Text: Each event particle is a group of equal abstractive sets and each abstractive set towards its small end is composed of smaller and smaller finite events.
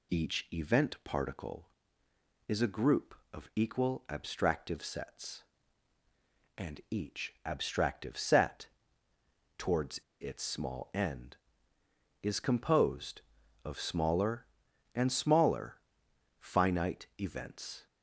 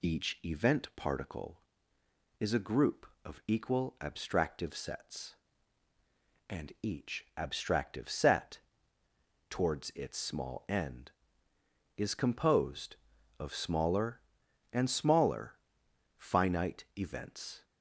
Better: second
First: pauses between "set" and "towards"; noticeable; at 8.6 s; 0.90 s long // pauses between "towards" and "its"; slight; at 9.9 s; 0.21 s long // pauses between "smaller" and "finite"; noticeable; at 15.7 s; 0.62 s long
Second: pauses between "set" and "towards"; noticeable; at 8.6 s; 0.90 s long // pauses between "smaller" and "finite"; noticeable; at 15.5 s; 0.62 s long

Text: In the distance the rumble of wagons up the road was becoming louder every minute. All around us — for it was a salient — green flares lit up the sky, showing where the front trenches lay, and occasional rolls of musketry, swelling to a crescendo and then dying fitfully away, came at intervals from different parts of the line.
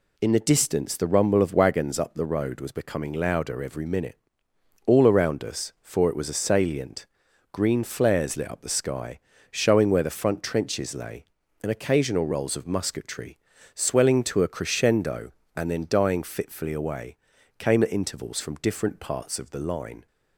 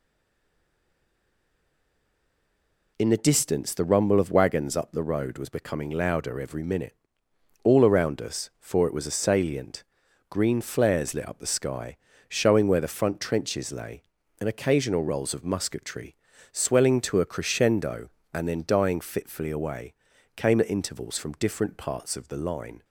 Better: first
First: none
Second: stays silent before the first word; strong; until 2.9 s; 2.9 s long

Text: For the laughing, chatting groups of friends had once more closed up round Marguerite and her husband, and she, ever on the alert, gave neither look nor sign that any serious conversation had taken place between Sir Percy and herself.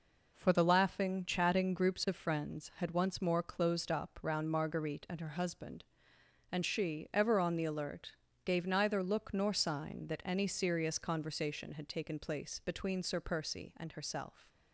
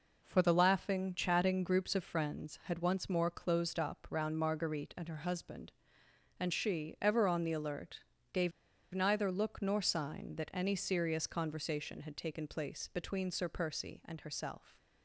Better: first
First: none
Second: pauses between "gave" and "neither"; at 8.5 s; 0.43 s long

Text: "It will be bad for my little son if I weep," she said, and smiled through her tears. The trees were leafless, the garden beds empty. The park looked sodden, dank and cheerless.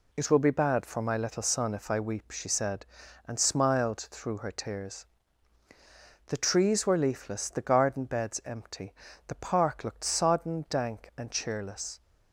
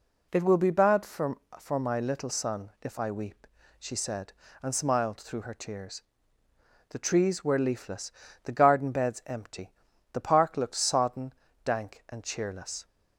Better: first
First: none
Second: says "for" twice; at 1.5 s

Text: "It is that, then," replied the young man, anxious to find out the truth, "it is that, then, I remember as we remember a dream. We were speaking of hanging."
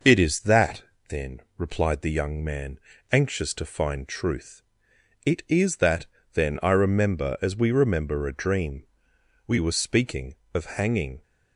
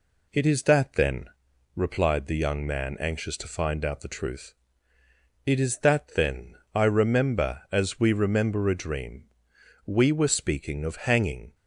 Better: second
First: skips "out the"; at 4.0 s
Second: none

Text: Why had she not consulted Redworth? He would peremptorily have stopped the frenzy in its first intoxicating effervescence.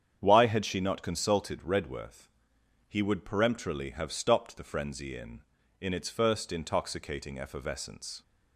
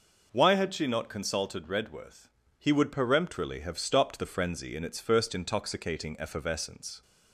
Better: second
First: starts louder than the rest; strong; until 1.2 s; 8.5 dB // says "in" twice; at 5.8 s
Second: none

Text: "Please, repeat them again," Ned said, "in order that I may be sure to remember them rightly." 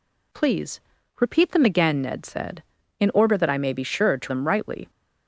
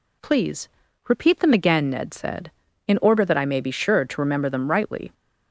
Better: second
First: skips "remember"; at 4.2 s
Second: none

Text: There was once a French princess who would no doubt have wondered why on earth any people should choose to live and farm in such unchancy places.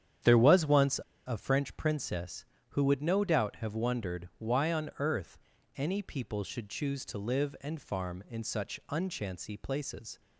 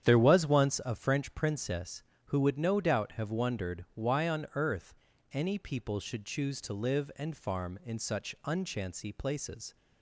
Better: second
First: starts louder than the rest; strong; until 1.4 s; 9 dB // pauses between "once" and "a"; slight; at 1.0 s; 0.24 s long // pauses between "earth" and "any"; at 5.3 s; 0.38 s long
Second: starts louder than the rest; strong; until 1.0 s; 9 dB // pauses between "earth" and "any"; at 4.9 s; 0.38 s long

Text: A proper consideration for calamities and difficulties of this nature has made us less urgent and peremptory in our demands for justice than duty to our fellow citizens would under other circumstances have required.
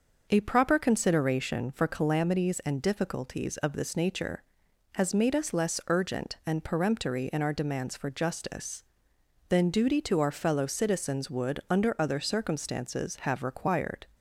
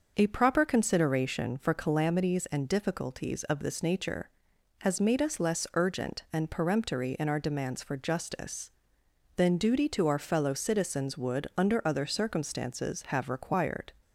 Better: neither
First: starts louder than the rest; noticeable; until 1.3 s; 6 dB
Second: starts louder than the rest; noticeable; until 1.1 s; 6 dB

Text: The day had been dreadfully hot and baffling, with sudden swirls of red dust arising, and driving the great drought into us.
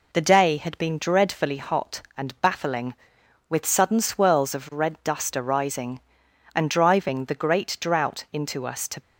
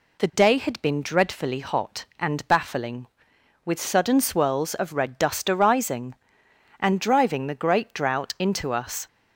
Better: second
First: goes on to say "To"; slight; from 8.8 s on; 0.14 s long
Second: none

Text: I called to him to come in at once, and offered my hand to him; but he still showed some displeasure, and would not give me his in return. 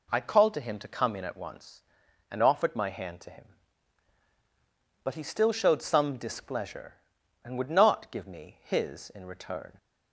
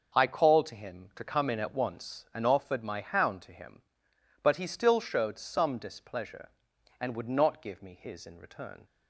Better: first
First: none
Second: starts louder than the rest; until 1.2 s; 6.5 dB // says "hound" for "hand"; at 3.0 s

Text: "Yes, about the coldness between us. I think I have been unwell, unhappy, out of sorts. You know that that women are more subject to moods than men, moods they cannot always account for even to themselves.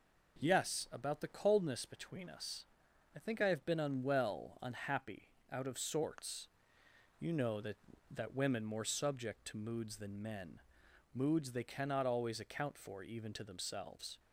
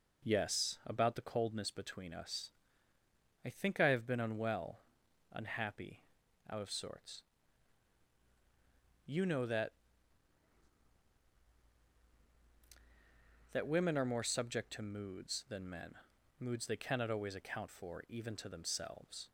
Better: second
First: skips "are"; at 8.6 s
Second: none

